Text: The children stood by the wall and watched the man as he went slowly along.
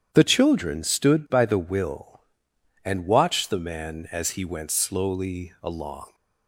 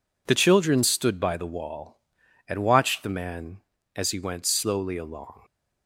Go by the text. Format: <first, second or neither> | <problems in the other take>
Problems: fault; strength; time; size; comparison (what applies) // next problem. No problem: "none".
second | starts louder than the rest; strong; until 1.1 s; 9 dB // says "will" for "wall"; at 1.5 s